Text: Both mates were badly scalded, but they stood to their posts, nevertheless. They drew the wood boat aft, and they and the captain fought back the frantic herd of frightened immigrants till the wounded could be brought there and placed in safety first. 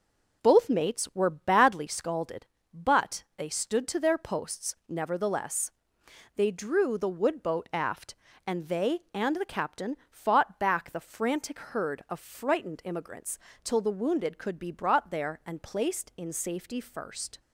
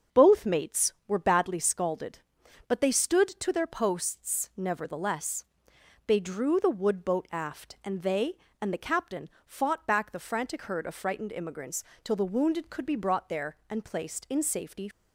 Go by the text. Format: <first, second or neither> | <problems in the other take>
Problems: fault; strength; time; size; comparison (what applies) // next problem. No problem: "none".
first | starts louder than the rest; until 1.2 s; 6 dB // pauses between "captain" and "fought"; slight; at 9.2 s; 0.16 s long // pauses between "immigrants" and "till"; slight; at 11.8 s; 0.20 s long; slight in the first // stops before "first"; at 14.9 s